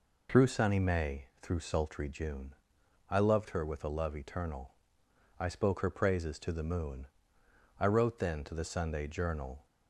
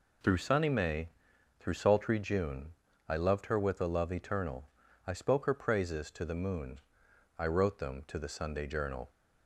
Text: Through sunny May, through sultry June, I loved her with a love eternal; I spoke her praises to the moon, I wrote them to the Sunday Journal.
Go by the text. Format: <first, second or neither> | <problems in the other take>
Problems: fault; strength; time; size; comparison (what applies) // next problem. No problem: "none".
second | says "then" for "them"; at 8.2 s